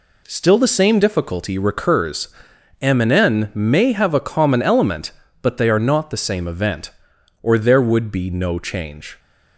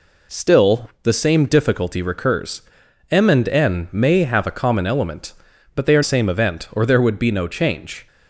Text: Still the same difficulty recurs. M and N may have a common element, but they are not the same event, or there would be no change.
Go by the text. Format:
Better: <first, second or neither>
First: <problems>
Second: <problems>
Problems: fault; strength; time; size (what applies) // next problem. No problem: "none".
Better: first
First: none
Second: skips "not the"; at 6.0 s